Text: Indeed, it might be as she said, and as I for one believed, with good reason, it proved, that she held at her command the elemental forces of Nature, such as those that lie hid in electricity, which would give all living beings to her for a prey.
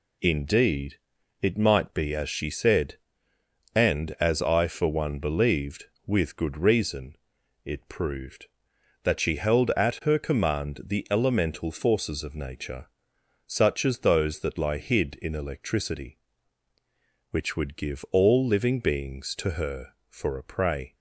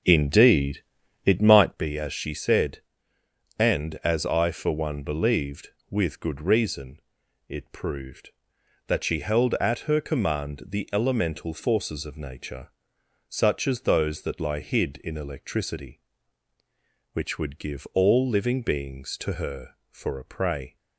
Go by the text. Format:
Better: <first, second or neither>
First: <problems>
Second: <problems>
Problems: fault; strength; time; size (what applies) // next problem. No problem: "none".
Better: first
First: none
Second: starts louder than the rest; noticeable; until 1.7 s; 6 dB